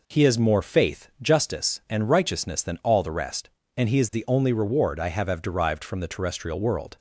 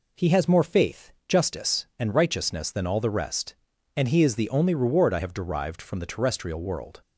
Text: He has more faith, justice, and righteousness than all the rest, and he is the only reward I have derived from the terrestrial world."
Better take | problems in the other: second | says "have" twice; at 5.2 s

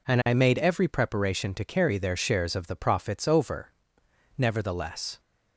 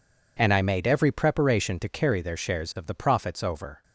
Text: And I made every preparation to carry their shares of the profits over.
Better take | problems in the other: second | goes on to say "Nevertheless"; noticeable; from 4.3 s on; 0.82 s long

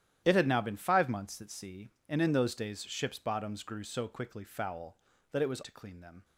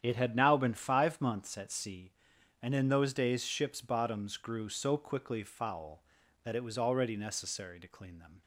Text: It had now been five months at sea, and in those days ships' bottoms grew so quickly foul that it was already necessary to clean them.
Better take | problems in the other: second | starts louder than the rest; strong; until 1.2 s; 11.5 dB; strong in the second // skips "already necessary"; at 5.6 s

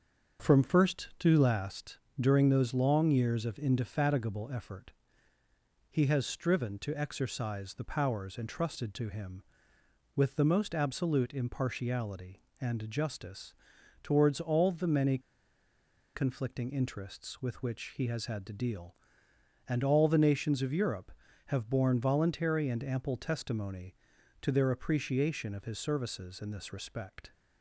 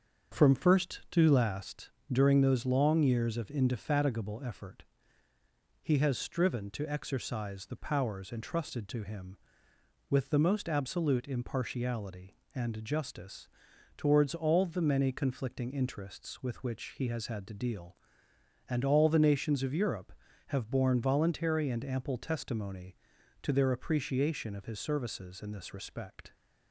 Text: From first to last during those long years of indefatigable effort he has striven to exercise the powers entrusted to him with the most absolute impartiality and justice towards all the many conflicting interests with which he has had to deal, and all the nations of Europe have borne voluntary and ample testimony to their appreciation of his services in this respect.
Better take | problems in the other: second | starts louder than the rest; until 1.5 s; 7 dB; also in the second // pauses between "last" and "during"; slight; at 1.9 s; 0.20 s long; slight in the second // pauses between "effort" and "he"; at 4.9 s; 1.0 s long; also in the second // pauses between "justice" and "towards"; noticeable; at 13.5 s; 0.48 s long; noticeable in the second // pauses between "many" and "conflicting"; noticeable; at 15.1 s; 0.96 s long

